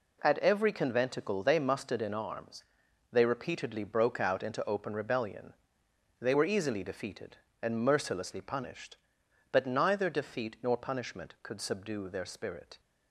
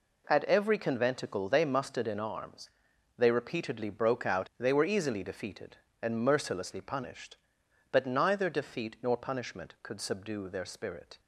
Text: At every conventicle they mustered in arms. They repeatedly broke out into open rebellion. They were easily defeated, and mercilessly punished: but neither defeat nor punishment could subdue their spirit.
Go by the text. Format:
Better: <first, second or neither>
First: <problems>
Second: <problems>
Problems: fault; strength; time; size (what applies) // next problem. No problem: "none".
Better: first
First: none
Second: skips "into open rebellion"; at 4.5 s